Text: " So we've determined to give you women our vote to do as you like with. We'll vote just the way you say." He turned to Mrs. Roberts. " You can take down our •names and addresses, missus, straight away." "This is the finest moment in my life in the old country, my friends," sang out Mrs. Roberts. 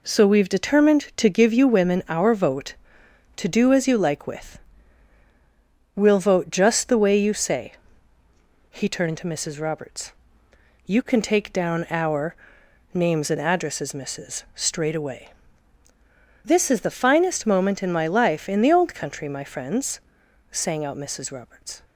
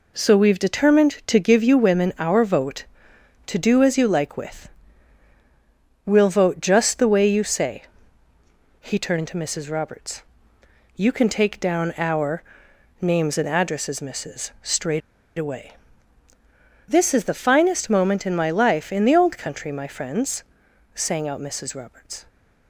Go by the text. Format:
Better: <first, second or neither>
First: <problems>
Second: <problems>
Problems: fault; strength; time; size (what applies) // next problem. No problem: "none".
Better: first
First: none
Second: pauses between "straight" and "away"; at 15.0 s; 0.38 s long